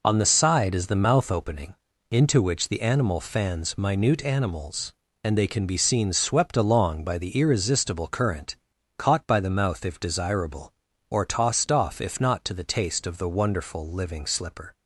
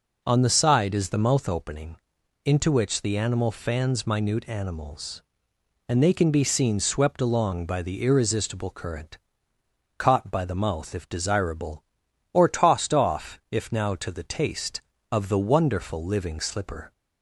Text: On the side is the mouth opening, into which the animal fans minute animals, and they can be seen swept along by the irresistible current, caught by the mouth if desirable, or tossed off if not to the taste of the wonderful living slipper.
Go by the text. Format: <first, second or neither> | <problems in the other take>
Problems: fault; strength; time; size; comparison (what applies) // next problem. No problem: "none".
first | says "now" for "not"; at 13.7 s